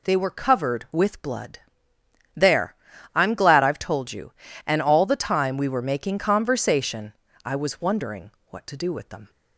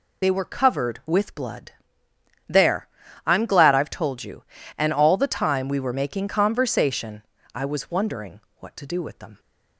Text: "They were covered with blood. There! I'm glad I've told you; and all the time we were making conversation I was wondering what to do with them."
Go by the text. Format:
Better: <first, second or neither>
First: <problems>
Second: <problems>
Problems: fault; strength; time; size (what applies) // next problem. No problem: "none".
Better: first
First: pauses between "conversation" and "I"; slight; at 7.1 s; 0.32 s long // pauses between "wondering" and "what"; slight; at 8.2 s; 0.20 s long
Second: loses the start of "They"; at 0.2 s; 35 ms // pauses between "conversation" and "I"; slight; at 7.2 s; 0.32 s long // pauses between "wondering" and "what"; slight; at 8.3 s; 0.20 s long